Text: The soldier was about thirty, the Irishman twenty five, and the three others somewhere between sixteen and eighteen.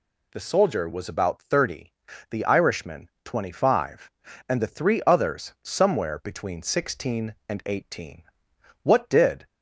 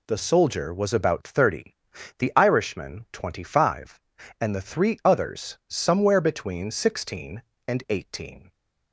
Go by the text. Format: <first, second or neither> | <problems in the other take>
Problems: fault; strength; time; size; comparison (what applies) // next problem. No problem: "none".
second | goes on to say "What did"; noticeable; from 8.8 s on; 0.64 s long